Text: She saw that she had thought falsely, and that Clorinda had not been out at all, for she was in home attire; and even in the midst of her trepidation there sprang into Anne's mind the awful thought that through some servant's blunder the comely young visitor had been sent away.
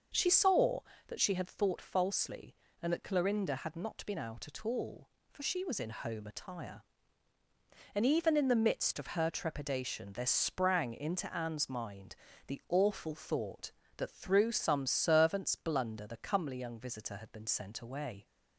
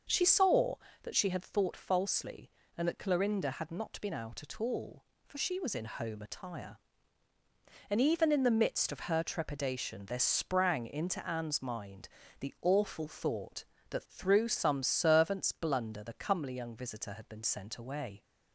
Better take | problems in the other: neither | starts louder than the rest; the same in both // pauses between "mind" and "the"; slight; the same in both

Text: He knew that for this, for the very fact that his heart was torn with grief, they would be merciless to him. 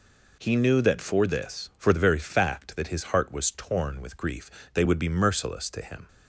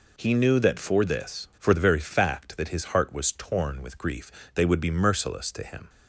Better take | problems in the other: neither | none

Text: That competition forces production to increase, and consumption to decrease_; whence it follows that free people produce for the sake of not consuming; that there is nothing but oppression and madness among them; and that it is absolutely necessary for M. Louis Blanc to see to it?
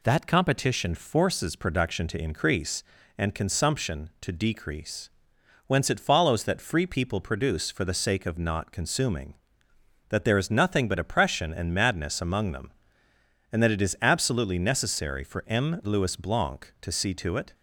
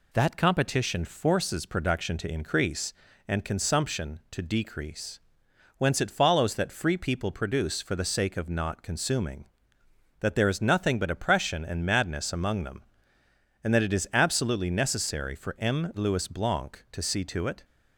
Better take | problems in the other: neither | none

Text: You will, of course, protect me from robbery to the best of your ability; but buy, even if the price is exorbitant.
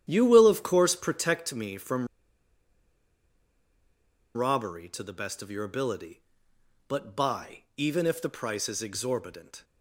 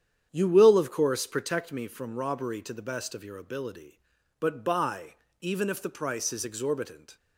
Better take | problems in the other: second | starts louder than the rest; strong; until 1.1 s; 10 dB; strong in the second // pauses between "from" and "robbery"; strong; at 2.0 s; 2.2 s long

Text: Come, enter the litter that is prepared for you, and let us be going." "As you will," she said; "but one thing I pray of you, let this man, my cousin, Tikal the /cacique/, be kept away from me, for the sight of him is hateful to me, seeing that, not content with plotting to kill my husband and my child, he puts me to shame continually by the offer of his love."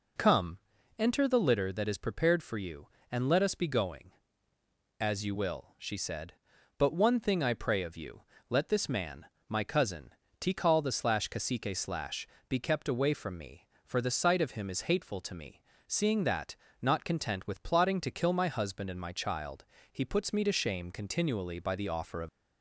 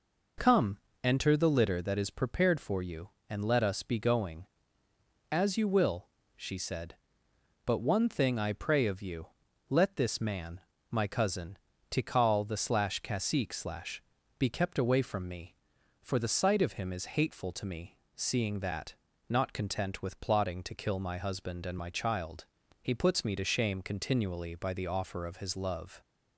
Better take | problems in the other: second | stops before "his love"; at 22.2 s

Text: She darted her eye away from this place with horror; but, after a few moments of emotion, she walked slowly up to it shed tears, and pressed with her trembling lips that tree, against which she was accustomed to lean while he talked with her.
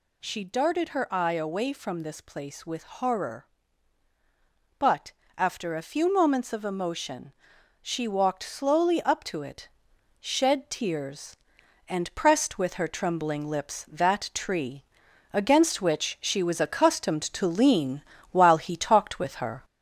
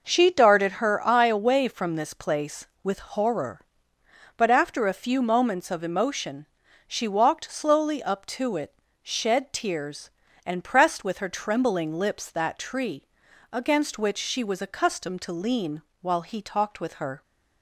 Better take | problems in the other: second | gets louder; throughout; 3.5 dB // pauses between "it" and "shed"; noticeable; at 9.6 s; 0.52 s long; slight in the second // pauses between "lean" and "while"; slight; at 18.0 s; 0.28 s long; slight in the second

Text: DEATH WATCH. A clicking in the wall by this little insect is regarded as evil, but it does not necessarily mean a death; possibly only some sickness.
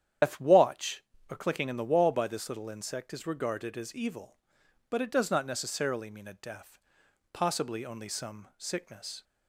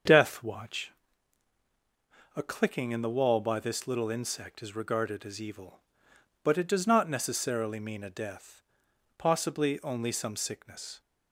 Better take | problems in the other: second | loses the start of "DEATH"; at 0.2 s; 130 ms // starts louder than the rest; strong; until 1.4 s; 9.5 dB; also in the second

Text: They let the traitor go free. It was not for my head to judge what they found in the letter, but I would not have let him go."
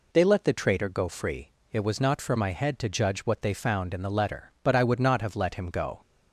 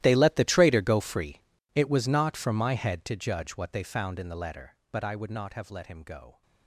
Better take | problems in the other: first | gets quieter; strong; throughout; 19.5 dB

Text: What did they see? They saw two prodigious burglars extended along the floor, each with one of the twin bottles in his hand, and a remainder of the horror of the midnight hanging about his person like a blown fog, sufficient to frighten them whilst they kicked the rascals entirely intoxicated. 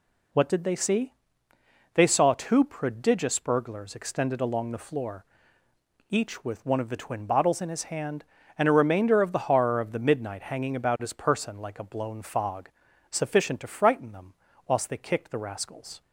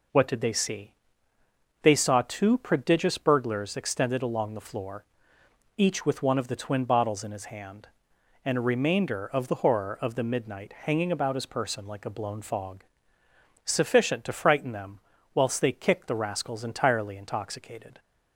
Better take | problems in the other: second | pauses between "them" and "whilst"; slight; at 14.3 s; 0.34 s long; slight in the second // stops before "entirely intoxicated"; at 16.0 s

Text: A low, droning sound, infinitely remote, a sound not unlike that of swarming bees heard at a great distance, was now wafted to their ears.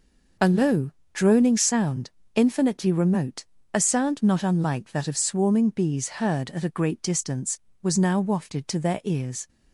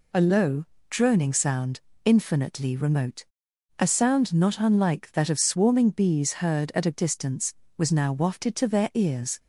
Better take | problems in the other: first | skips "great"; at 6.9 s

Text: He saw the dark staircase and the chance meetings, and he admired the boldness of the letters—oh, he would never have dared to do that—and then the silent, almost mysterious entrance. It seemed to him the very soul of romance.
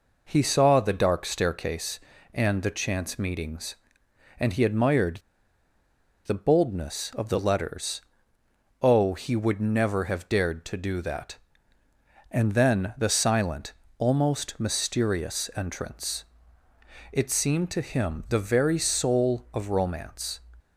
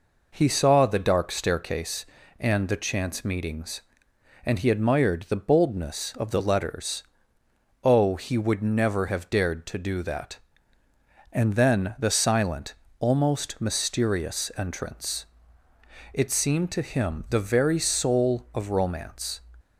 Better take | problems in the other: second | pauses between "admired" and "the"; at 5.1 s; 1.0 s long

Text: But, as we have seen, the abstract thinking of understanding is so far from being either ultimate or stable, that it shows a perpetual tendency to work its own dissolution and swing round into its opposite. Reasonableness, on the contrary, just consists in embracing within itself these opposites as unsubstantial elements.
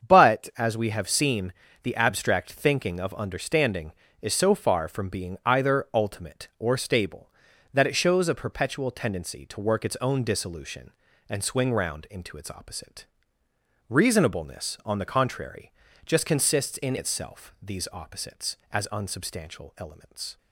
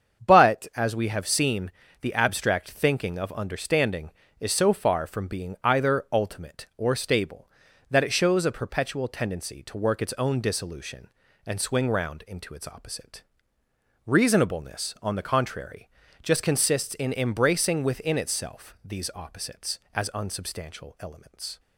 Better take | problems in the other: second | starts louder than the rest; strong; until 1.1 s; 7 dB; strong in the second // skips "embracing within"; at 16.9 s

